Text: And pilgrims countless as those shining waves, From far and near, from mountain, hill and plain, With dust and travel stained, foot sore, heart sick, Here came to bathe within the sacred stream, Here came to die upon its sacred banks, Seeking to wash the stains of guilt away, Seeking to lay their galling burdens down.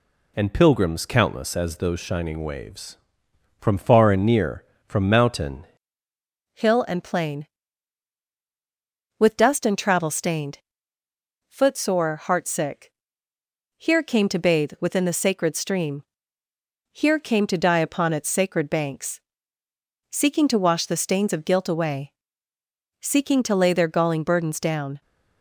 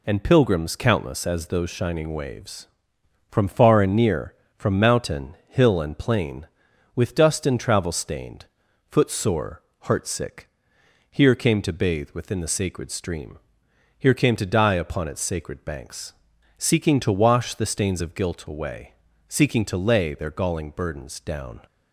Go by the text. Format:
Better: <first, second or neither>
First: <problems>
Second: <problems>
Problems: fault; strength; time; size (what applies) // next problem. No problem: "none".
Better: second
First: changes voice at "hill"; from 6.5 s on; 18.5 s long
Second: none